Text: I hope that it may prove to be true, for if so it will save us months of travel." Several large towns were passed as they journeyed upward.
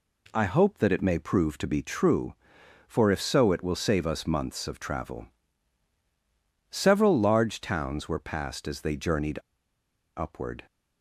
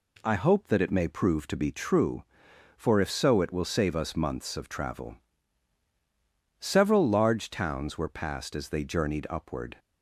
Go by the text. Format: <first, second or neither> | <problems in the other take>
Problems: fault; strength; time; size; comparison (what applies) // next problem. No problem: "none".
second | pauses between "journeyed" and "upward"; noticeable; at 9.3 s; 0.77 s long